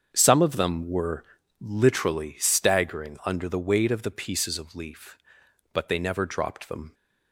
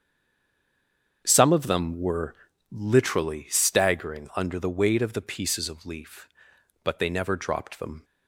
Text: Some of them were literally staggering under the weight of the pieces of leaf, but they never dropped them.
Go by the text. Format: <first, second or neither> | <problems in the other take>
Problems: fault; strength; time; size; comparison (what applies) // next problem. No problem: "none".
first | stays silent before the first word; noticeable; until 1.2 s; 1.2 s long // starts louder than the rest; strong; until 2.2 s; 7.5 dB; strong in the first // pauses between "were" and "literally"; slight; at 2.3 s; 0.36 s long; slight in the first